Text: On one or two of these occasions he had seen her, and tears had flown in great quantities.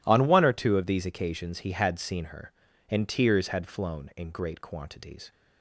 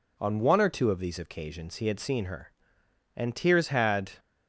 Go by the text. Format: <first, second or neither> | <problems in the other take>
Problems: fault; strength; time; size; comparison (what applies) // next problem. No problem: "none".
first | stops before "flown in great quantities"; at 4.1 s